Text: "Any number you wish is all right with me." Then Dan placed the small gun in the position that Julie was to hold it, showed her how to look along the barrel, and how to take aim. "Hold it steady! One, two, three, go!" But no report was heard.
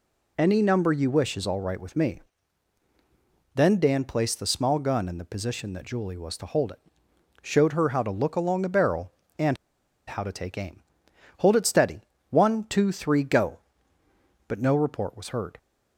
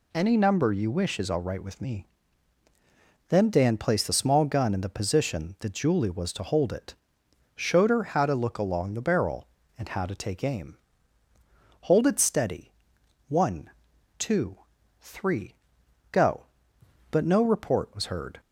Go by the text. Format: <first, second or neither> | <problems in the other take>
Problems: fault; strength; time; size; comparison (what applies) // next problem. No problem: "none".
second | pauses between "and" and "how"; noticeable; at 9.5 s; 0.53 s long